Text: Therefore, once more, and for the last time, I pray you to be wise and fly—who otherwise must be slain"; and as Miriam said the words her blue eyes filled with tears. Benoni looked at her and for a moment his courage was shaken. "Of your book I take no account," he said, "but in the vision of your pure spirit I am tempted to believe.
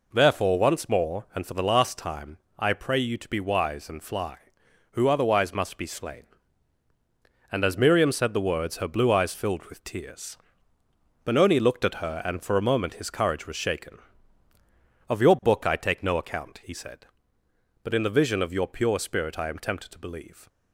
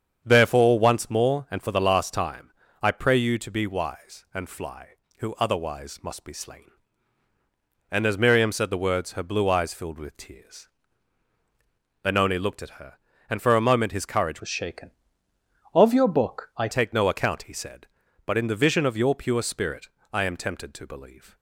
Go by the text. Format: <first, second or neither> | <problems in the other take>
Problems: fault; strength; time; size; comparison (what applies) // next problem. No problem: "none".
first | starts louder than the rest; strong; until 1.2 s; 8 dB // changes voice from "was" to "I"; from 14.4 to 16.6 s; 2.2 s long // pauses between "spirit" and "I"; slight; at 19.8 s; 0.24 s long